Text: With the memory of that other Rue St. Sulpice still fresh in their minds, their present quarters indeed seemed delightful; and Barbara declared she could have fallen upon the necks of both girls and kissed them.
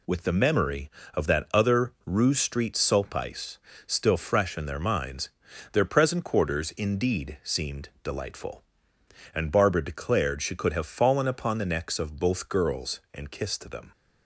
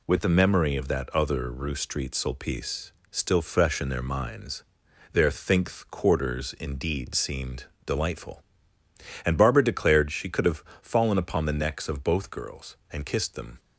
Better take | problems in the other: first | pauses between "Sulpice" and "still"; slight; at 2.9 s; 0.18 s long; slight in the first // says "thinkth" for "present"; at 5.3 s // pauses between "seemed" and "delightful"; slight; at 7.6 s; 0.18 s long // pauses between "have" and "fallen"; slight; at 10.6 s; 0.20 s long

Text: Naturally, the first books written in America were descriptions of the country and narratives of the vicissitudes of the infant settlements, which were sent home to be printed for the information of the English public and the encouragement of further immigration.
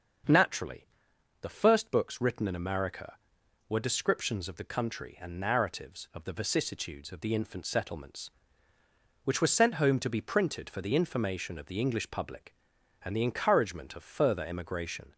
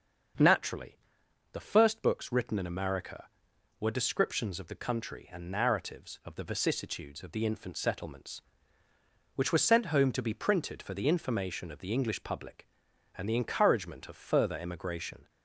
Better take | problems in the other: neither | starts louder than the rest; the same in both

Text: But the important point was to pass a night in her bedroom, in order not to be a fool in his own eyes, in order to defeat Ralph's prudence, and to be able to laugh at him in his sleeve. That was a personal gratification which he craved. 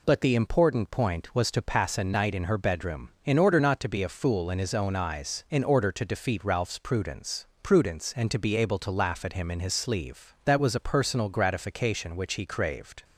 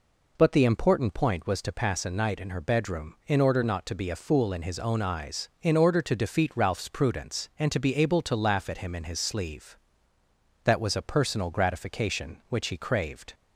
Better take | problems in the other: second | says "prudence" twice; at 7.6 s

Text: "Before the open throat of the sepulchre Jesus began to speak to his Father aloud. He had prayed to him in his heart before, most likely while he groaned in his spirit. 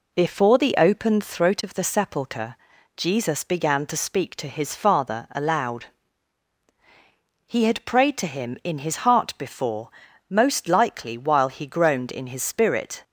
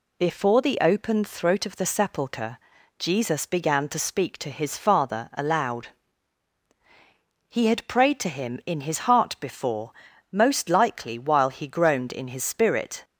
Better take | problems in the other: second | starts louder than the rest; slight; until 1.6 s; 2.5 dB // pauses between "sepulchre" and "Jesus"; at 2.5 s; 0.40 s long; also in the second

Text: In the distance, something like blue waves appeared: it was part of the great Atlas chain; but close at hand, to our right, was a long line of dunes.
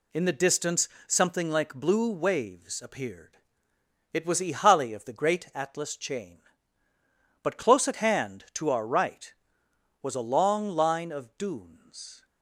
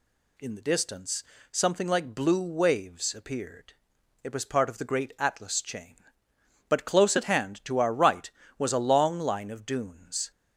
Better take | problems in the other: second | says "ihali" for "part"; at 4.4 s

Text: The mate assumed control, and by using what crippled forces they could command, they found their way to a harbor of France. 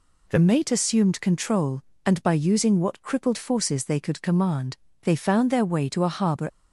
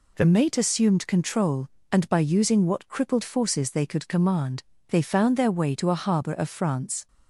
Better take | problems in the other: second | stops before "of France"; at 6.4 s

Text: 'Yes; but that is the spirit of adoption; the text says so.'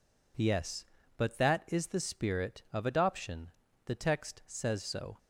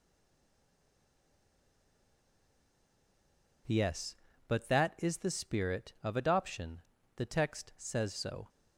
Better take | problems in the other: first | stays silent before the first word; strong; until 3.6 s; 3.6 s long

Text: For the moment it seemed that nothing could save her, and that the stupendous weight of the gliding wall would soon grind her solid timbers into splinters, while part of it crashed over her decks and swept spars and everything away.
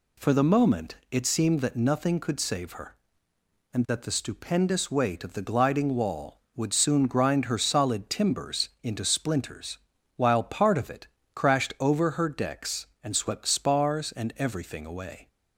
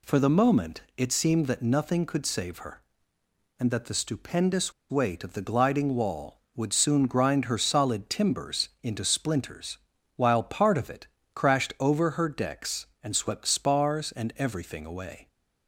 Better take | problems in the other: first | pauses between "moment" and "it"; slight; at 0.8 s; 0.16 s long; slight in the first // pauses between "stupendous" and "weight"; slight; at 4.7 s; 0.18 s long // pauses between "it" and "crashed"; slight; at 11.0 s; 0.26 s long; slight in the first

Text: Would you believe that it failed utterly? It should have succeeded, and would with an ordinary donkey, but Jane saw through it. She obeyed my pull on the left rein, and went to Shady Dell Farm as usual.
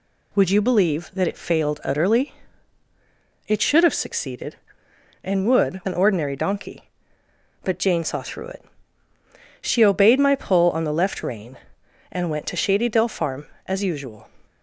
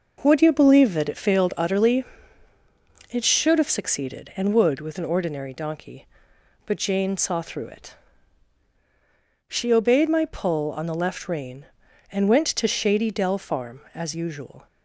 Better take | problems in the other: second | skips "with"; at 5.8 s

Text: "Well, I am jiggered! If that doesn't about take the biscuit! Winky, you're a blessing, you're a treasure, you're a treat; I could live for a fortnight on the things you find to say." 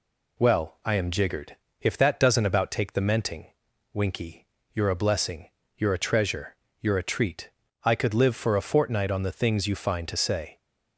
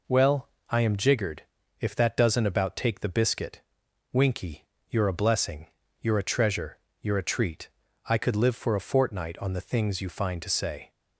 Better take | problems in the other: second | says "menting" for "biscuit"; at 3.0 s

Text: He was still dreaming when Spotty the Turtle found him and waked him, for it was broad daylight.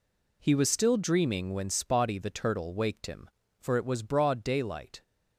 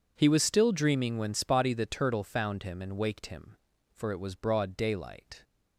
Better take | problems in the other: second | skips "found him and"; at 2.7 s

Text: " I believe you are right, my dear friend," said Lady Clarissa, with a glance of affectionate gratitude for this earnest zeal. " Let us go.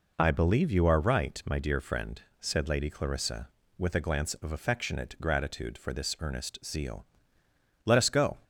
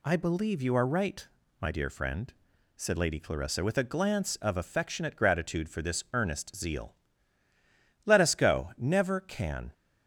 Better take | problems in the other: first | goes on to say "Never can"; noticeable; from 8.7 s on; 0.96 s long

